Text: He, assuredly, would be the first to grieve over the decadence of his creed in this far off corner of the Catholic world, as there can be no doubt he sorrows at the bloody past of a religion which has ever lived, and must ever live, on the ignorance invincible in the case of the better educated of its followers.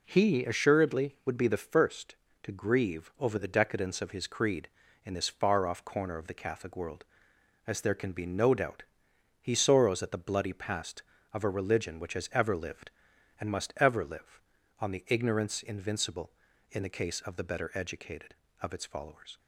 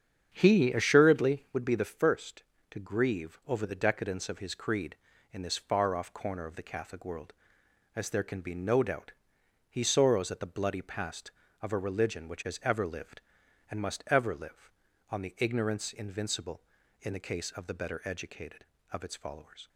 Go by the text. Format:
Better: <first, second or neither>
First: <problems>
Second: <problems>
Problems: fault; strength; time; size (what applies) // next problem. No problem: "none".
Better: first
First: pauses between "doubt" and "he"; noticeable; at 8.8 s; 0.56 s long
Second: starts louder than the rest; strong; until 1.6 s; 8 dB // pauses between "doubt" and "he"; noticeable; at 9.1 s; 0.56 s long